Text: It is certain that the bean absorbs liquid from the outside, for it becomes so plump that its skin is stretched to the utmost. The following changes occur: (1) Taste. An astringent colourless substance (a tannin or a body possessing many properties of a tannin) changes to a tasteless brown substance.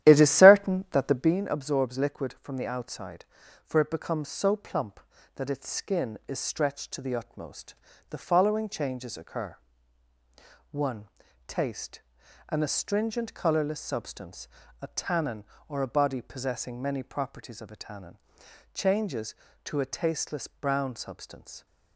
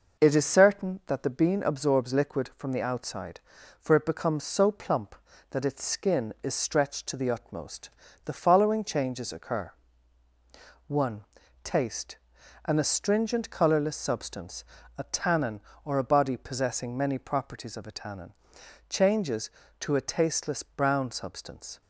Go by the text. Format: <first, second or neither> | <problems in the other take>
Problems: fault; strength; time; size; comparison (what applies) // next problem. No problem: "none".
second | starts louder than the rest; strong; until 1.4 s; 12 dB